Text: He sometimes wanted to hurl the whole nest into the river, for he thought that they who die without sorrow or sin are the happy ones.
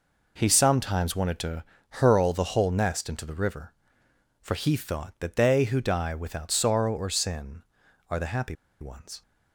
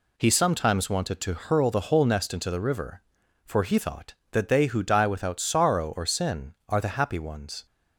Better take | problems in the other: second | pauses between "to" and "hurl"; slight; at 1.6 s; 0.28 s long // pauses between "happy" and "ones"; slight; at 8.5 s; 0.26 s long

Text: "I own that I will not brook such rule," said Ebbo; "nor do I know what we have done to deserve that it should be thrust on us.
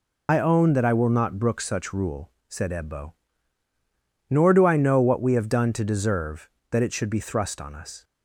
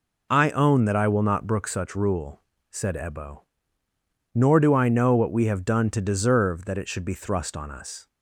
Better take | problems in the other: second | loses the start of "I"; at 0.2 s; 75 ms

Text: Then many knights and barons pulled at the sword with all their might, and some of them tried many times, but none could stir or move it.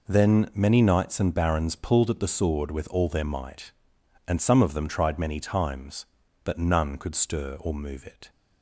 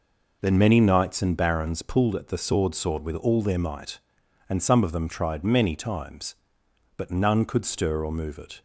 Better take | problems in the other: first | says "sword" twice; at 2.7 s

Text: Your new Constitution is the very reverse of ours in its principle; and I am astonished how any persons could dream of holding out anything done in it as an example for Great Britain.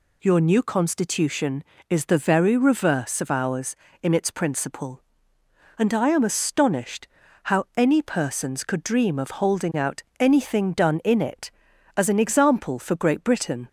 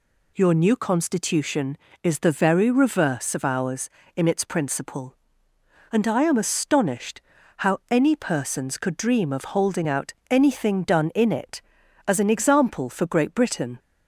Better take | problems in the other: neither | pauses between "astonished" and "how"; slight; the same in both // pauses between "out" and "anything"; slight; the same in both

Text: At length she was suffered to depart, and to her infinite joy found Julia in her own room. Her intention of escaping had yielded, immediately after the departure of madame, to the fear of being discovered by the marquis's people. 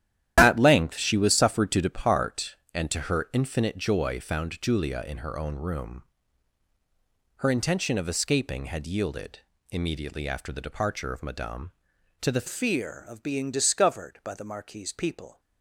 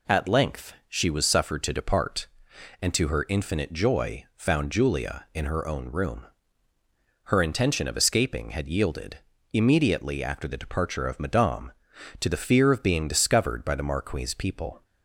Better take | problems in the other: second | starts louder than the rest; strong; until 1.3 s; 11.5 dB // changes voice at "fear"; from 12.4 s on; 2.9 s long

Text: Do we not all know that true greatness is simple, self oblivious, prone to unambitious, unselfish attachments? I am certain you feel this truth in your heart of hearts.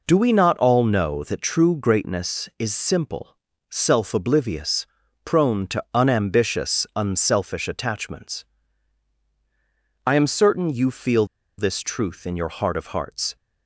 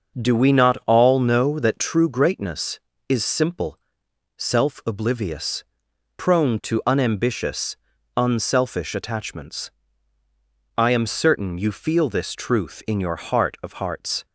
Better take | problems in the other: second | pauses between "feel" and "this"; slight; at 11.2 s; 0.33 s long

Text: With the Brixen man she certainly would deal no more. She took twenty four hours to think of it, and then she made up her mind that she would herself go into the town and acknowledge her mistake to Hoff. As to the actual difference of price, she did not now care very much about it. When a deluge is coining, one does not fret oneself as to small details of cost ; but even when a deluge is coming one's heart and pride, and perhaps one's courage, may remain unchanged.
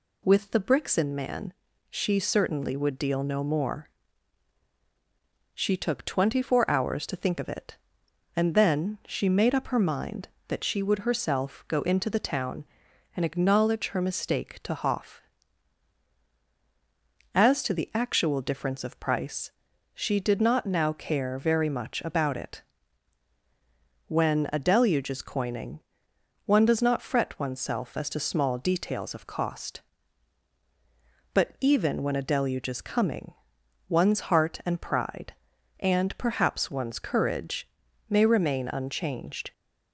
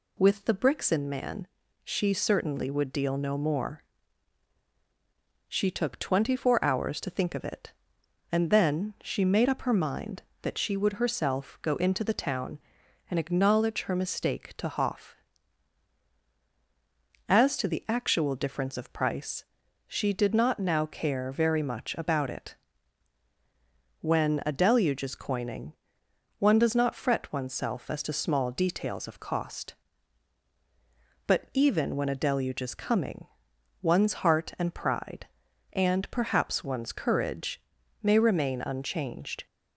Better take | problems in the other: neither | pauses between "man" and "she"; the same in both // pauses between "coming" and "one's"; noticeable; the same in both

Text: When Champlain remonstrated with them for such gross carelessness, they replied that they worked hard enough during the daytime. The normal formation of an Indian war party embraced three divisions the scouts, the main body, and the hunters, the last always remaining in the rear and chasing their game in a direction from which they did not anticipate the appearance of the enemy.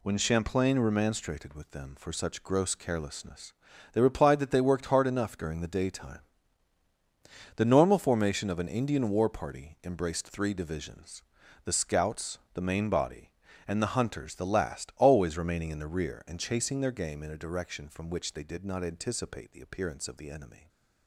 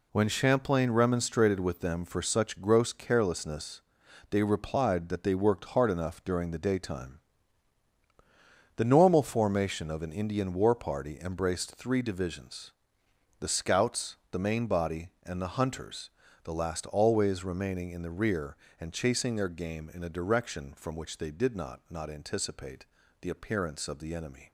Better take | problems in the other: first | pauses between "divisions" and "the"; noticeable; at 12.7 s; 0.68 s long; also in the first // says "not" twice; at 21.8 s // pauses between "anticipate" and "the"; slight; at 22.8 s; 0.36 s long

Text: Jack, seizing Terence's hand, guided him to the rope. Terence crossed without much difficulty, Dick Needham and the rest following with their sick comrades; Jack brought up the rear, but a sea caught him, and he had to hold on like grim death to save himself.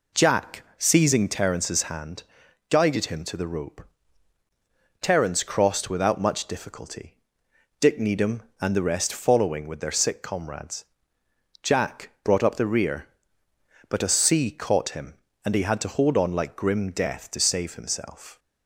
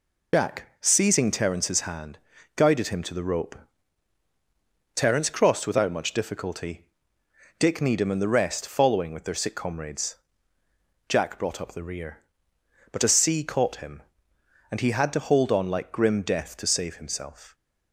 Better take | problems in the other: first | loses the start of "Jack"; at 0.3 s; 70 ms

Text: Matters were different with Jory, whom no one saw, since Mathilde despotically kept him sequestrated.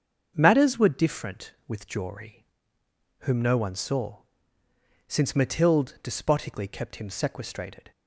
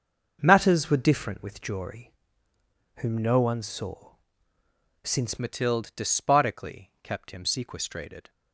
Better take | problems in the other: first | starts louder than the rest; until 1.4 s; 6.5 dB; also in the first // changes voice at "Mathilde"; from 5.3 s on; 2.9 s long

